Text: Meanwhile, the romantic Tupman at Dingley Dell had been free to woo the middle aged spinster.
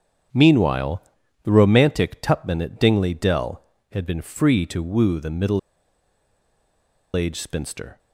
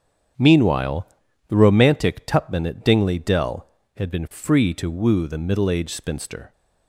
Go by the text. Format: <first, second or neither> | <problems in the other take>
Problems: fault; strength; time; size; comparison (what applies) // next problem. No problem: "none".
second | starts louder than the rest; strong; until 1.7 s; 8 dB; strong in the second // pauses between "middle" and "aged"; strong; at 5.5 s; 1.5 s long